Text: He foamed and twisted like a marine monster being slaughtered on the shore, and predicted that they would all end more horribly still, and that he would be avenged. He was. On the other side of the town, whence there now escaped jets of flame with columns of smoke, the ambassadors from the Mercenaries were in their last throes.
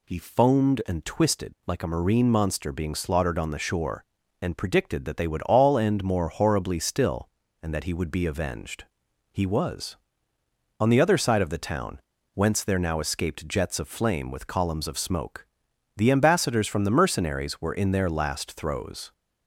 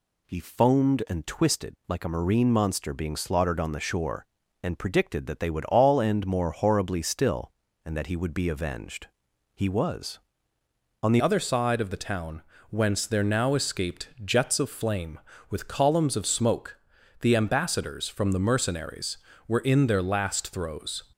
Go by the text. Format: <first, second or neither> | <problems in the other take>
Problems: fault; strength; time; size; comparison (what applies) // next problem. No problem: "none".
first | changes voice at "other"; from 11.2 s on; 9.8 s long